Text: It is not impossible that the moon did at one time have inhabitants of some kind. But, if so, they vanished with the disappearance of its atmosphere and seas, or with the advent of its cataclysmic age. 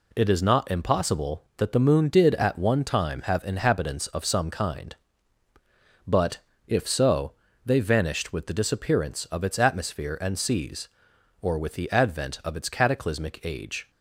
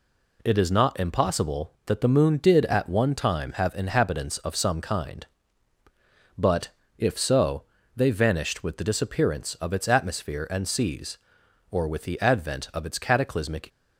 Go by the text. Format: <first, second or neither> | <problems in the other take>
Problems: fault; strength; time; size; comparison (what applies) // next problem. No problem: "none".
first | stops before "age"; at 13.6 s